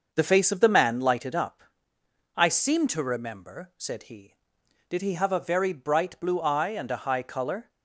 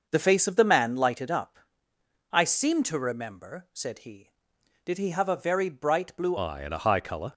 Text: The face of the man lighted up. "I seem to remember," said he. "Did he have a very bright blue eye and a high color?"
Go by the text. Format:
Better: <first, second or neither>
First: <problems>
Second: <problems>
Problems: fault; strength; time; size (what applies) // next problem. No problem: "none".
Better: first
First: starts louder than the rest; noticeable; until 1.1 s; 6 dB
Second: starts louder than the rest; noticeable; until 1.1 s; 6 dB // changes voice at "eye"; from 6.3 s on; 1.0 s long